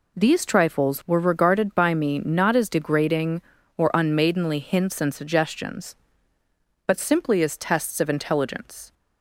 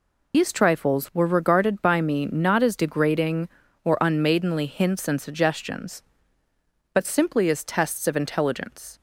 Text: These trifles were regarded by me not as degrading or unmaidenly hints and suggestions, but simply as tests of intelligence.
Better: first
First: none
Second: loses the start of "These"; at 0.3 s; 125 ms

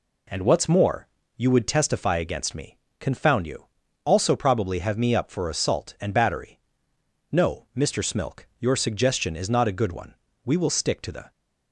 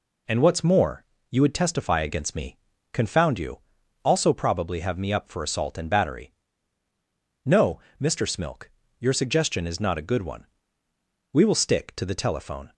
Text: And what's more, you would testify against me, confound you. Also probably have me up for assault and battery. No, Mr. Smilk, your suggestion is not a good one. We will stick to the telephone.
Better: second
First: stops before "telephone"; at 11.3 s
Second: none

